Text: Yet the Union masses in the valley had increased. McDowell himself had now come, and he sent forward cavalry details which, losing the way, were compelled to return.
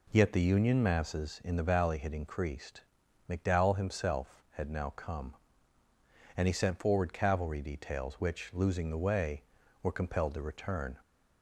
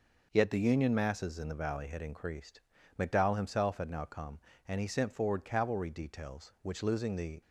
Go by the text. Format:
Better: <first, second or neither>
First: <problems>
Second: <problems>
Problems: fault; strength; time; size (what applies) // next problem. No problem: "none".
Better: first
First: none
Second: stops before "way were compelled to return"; at 7.4 s